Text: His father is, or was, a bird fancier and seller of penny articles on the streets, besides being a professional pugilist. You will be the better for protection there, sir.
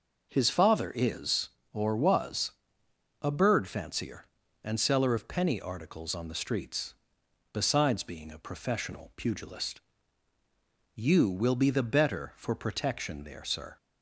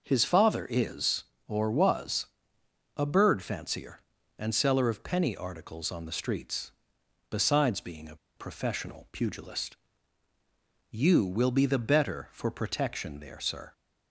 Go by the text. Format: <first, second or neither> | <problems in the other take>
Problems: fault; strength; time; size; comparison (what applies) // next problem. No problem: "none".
first | pauses between "a" and "professional"; slight; at 8.1 s; 0.20 s long